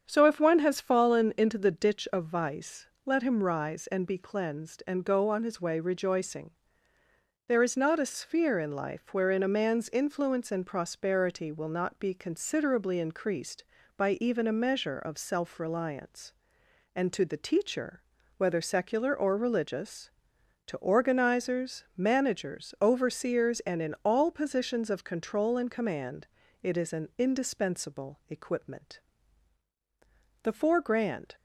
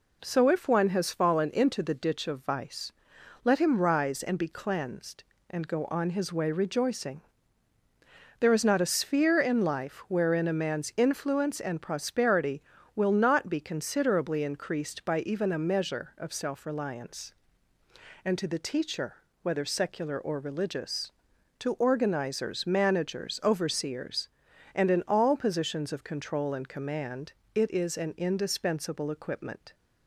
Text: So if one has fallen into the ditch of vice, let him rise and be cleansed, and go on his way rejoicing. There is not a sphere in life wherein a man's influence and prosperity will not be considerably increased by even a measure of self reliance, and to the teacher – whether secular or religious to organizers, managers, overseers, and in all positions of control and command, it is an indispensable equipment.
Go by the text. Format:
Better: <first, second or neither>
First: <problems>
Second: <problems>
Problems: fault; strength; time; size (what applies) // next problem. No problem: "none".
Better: second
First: starts louder than the rest; strong; until 1.0 s; 7.5 dB // goes on to say "The four grand"; noticeable; from 30.4 s on; 0.94 s long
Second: none